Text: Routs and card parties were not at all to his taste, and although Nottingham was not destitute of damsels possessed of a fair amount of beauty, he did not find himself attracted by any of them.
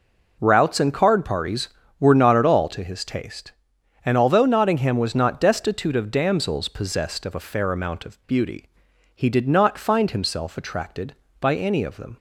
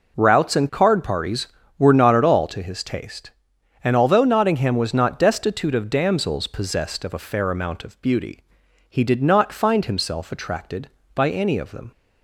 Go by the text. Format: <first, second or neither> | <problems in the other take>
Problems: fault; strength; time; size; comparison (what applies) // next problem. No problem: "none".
neither | none